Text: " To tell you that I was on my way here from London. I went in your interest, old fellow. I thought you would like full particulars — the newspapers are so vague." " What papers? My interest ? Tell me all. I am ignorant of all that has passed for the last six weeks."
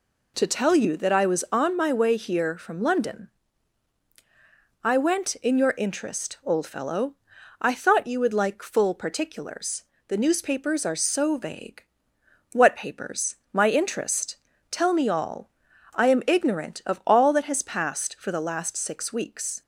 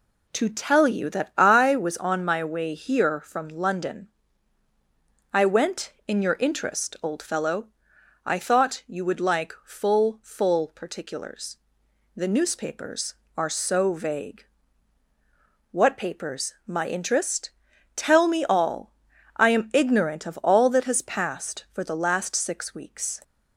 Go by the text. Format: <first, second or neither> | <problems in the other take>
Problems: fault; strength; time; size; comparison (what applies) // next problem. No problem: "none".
first | says "full" twice; at 10.2 s